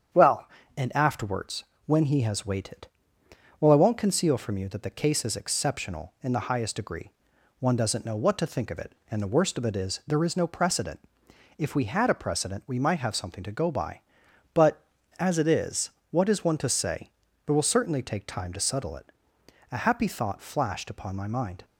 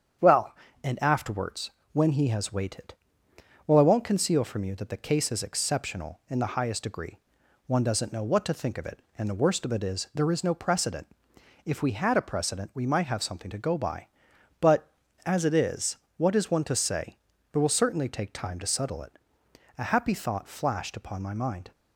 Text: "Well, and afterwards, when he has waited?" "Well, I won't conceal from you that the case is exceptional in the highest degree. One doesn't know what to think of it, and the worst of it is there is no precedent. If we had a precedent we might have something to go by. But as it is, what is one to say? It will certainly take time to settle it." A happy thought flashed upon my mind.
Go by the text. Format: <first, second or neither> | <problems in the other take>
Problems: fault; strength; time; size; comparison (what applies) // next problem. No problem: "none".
neither | starts louder than the rest; strong; the same in both